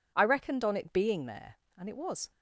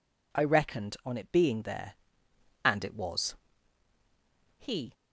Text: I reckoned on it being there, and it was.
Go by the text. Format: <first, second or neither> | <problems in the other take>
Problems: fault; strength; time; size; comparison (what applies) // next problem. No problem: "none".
first | goes on to say "He"; slight; from 4.5 s on; 0.34 s long